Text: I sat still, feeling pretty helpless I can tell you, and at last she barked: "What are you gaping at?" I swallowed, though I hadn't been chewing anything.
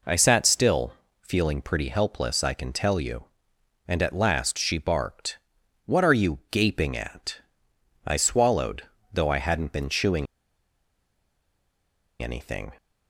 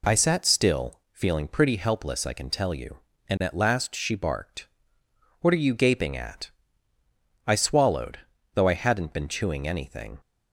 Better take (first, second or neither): second